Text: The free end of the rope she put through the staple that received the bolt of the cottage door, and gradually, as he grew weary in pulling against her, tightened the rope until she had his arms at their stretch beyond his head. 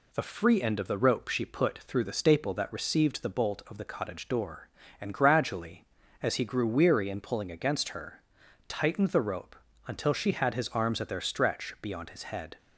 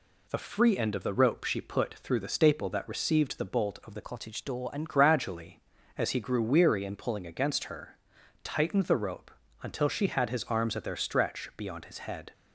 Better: first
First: pauses between "rope" and "until"; slight; at 9.5 s; 0.32 s long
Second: changes voice from "cottage" to "and"; from 4.0 to 4.8 s; 0.8 s long // pauses between "rope" and "until"; slight; at 9.3 s; 0.32 s long

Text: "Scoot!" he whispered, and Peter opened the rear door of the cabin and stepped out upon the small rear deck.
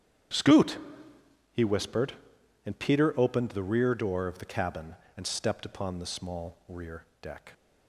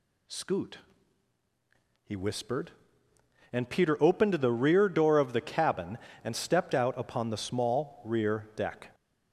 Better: second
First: starts louder than the rest; strong; until 2.0 s; 10 dB // skips "out"; at 5.6 s // pauses between "rear" and "deck"; slight; at 7.0 s; 0.16 s long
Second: none

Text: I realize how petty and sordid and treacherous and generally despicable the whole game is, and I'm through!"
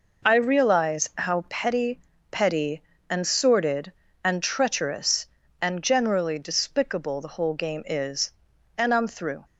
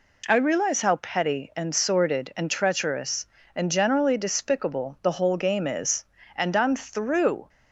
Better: second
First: says "petty" twice; at 2.3 s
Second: none

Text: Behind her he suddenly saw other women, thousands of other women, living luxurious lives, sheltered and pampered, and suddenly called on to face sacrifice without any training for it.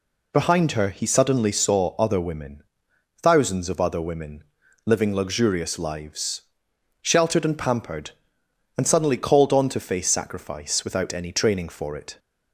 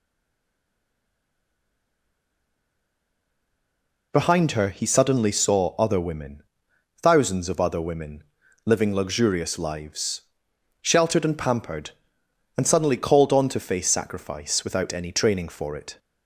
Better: first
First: none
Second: stays silent before the first word; strong; until 4.1 s; 4.1 s long

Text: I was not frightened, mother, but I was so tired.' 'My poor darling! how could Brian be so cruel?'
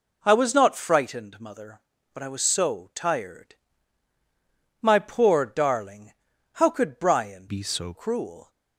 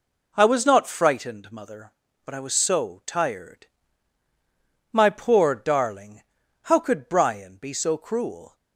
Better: second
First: changes voice from "be" to "so"; from 7.4 to 7.9 s; 0.5 s long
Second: none

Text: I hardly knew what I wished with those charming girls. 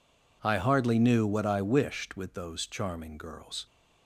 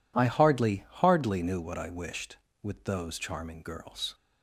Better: first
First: none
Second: says "hardly" twice; at 0.8 s

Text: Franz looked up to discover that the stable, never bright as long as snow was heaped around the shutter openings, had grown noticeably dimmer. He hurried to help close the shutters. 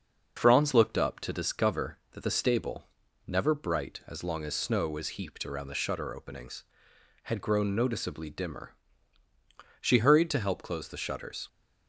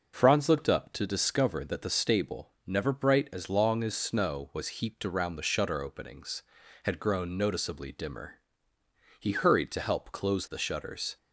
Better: second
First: starts louder than the rest; until 1.4 s; 6 dB // says "She" for "He"; at 9.7 s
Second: none

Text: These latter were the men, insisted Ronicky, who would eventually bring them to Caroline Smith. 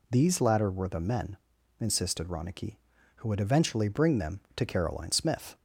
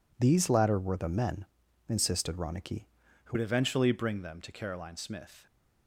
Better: first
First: none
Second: changes voice at "would"; from 3.3 s on; 2.1 s long

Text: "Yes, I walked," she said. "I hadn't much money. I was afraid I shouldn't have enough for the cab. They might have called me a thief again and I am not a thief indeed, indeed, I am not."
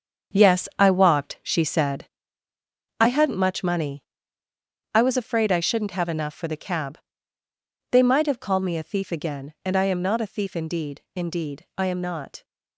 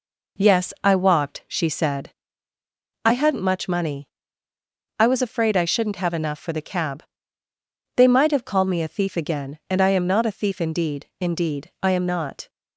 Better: second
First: gets quieter; strong; throughout; 9 dB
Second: none

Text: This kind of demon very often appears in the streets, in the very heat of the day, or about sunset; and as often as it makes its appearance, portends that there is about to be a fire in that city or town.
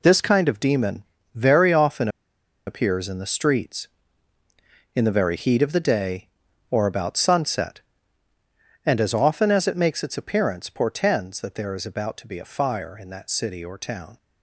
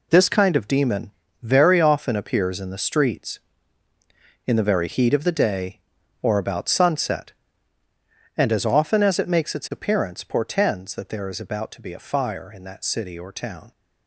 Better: second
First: pauses between "demon" and "very"; slight; at 1.0 s; 0.32 s long // pauses between "often" and "appears"; noticeable; at 2.0 s; 0.58 s long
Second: pauses between "demon" and "very"; slight; at 1.1 s; 0.32 s long

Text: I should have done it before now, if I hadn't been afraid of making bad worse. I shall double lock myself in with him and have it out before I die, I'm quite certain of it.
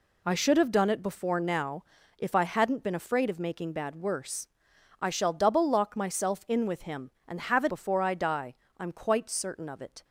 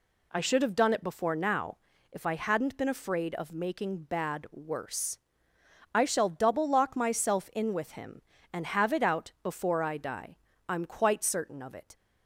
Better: second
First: skips "out"; at 7.6 s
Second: none

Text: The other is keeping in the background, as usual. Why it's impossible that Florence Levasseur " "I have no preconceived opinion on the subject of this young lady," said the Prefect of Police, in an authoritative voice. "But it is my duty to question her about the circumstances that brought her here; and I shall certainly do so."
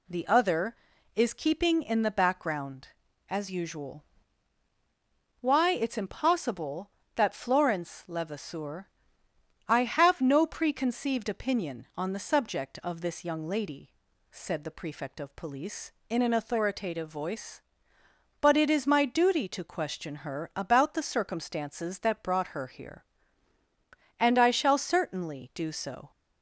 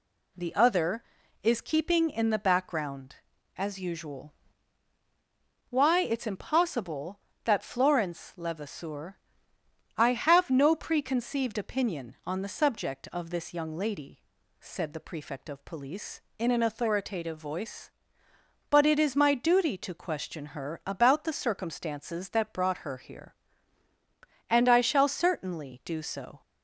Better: neither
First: none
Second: none

